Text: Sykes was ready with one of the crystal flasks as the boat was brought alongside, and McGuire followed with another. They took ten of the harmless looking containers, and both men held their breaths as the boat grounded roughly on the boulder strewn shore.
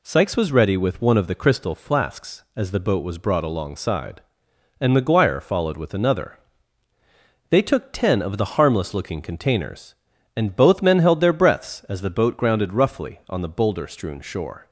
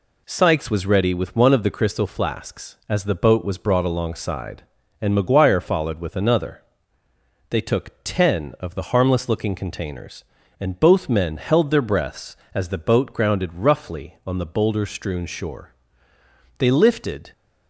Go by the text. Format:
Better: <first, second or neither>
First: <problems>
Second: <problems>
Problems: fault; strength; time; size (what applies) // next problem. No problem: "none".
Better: first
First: none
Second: goes on to say "They lifted"; noticeable; from 16.5 s on; 0.72 s long